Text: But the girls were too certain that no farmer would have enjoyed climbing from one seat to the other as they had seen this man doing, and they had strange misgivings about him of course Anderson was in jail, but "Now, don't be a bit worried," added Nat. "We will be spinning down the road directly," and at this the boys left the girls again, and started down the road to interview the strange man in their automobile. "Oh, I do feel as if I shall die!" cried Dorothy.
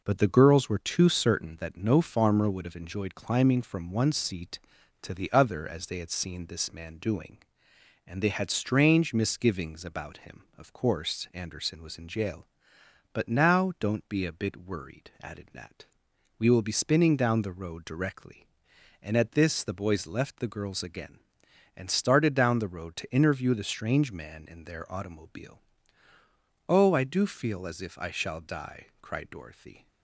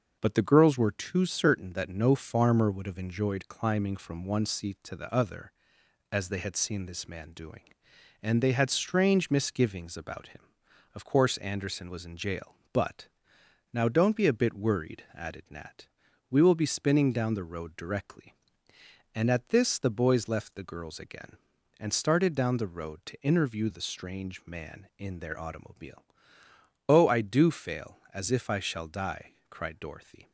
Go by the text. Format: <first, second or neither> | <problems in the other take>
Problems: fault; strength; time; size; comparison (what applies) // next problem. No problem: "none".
first | pauses between "but" and "Now"; noticeable; at 13.0 s; 0.66 s long // says "fail" for "feel"; at 27.4 s